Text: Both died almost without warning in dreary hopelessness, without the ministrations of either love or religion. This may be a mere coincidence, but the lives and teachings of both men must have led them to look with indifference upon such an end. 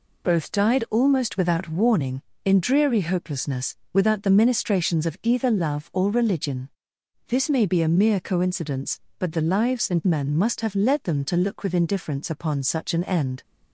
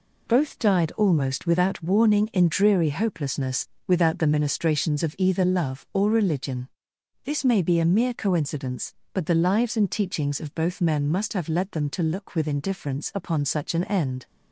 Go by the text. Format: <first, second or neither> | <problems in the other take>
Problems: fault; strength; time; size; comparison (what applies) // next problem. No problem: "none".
second | skips "teachings of both"; at 10.0 s